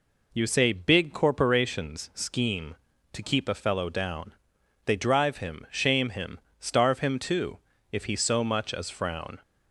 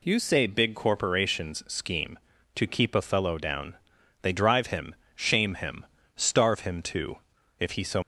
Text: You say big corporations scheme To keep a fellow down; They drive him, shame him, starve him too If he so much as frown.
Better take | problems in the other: first | pauses between "too" and "If"; at 7.1 s; 0.42 s long; slight in the first // stops before "much as frown"; at 8.0 s

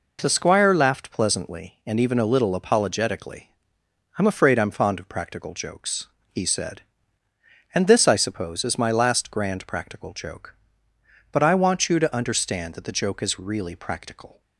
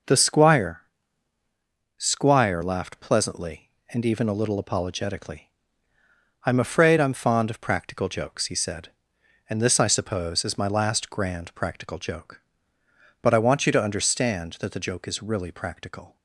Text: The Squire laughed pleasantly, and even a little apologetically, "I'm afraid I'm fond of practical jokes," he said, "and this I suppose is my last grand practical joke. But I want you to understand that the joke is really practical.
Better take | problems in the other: first | says "Squire" twice; at 1.9 s

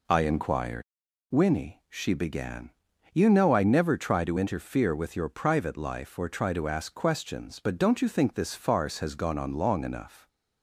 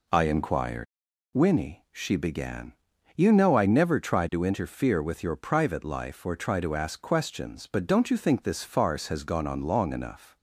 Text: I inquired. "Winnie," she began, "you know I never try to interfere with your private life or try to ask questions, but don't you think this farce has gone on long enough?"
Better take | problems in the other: neither | none

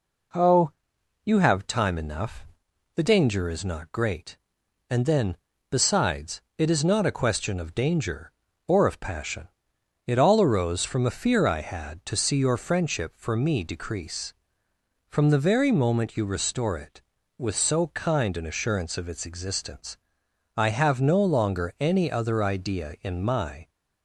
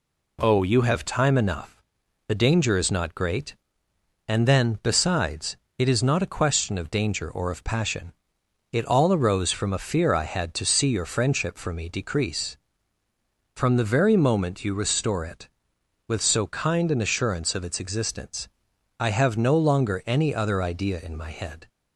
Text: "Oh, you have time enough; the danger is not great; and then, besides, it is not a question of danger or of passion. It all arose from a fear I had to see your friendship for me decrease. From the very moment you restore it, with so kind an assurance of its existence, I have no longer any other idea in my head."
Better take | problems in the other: second | stops before "head"; at 23.6 s

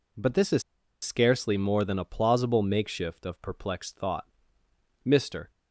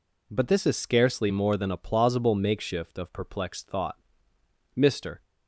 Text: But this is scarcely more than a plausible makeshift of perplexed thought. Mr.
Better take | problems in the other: second | pauses between "is" and "scarcely"; at 0.6 s; 0.40 s long

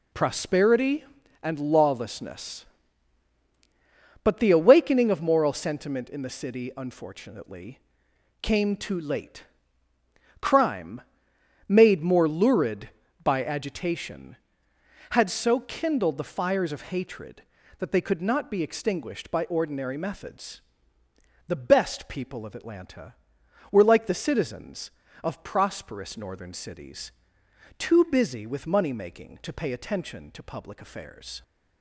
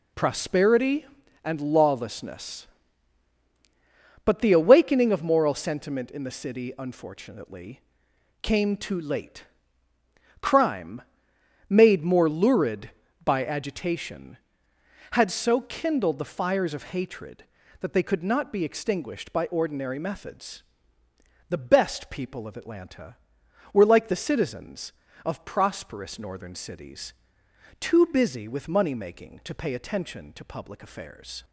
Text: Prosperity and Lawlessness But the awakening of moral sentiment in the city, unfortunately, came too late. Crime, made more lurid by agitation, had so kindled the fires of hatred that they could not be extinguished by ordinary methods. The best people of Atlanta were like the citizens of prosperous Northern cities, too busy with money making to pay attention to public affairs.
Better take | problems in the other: neither | none

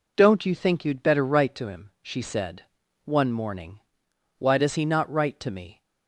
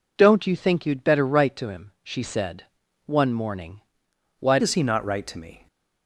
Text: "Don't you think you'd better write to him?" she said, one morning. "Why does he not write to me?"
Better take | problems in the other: first | changes voice at "does"; from 4.5 s on; 1.1 s long

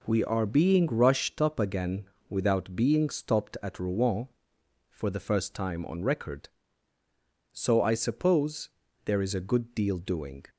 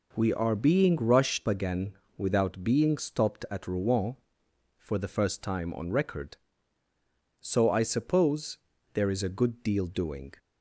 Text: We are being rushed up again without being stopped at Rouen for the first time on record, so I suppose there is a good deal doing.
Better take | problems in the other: first | skips "up"; at 1.4 s // pauses between "again" and "without"; slight; at 1.9 s; 0.22 s long; slight in the first // pauses between "suppose" and "there"; slight; at 8.5 s; 0.36 s long; slight in the first

